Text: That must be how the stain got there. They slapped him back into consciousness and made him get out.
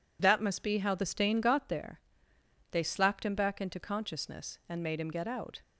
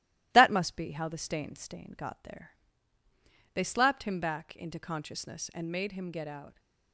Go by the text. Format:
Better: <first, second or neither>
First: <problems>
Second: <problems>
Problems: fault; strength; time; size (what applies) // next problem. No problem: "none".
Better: first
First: none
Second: starts louder than the rest; strong; until 1.3 s; 16 dB // says "stain" twice; at 1.5 s